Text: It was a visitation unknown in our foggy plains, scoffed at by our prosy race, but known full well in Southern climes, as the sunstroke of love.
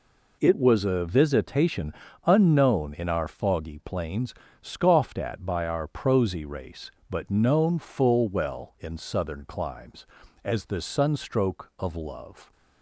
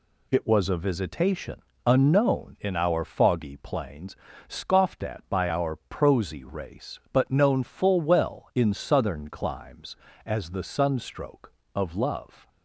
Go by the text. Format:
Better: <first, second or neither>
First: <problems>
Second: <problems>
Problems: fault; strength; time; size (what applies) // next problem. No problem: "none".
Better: neither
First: pauses between "visitation" and "unknown"; slight; at 1.9 s; 0.34 s long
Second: pauses between "visitation" and "unknown"; slight; at 1.6 s; 0.24 s long